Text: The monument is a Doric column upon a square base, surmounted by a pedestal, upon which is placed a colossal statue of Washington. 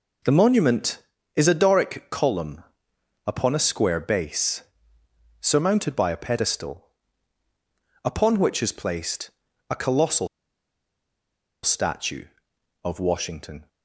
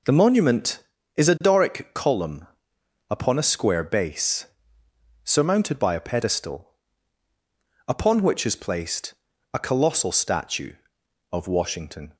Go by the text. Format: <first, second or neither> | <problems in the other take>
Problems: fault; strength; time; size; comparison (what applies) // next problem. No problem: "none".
second | pauses between "column" and "upon"; noticeable; at 2.6 s; 0.64 s long; noticeable in the second // pauses between "placed" and "a"; at 9.3 s; 0.38 s long; also in the second // pauses between "colossal" and "statue"; strong; at 10.2 s; 1.3 s long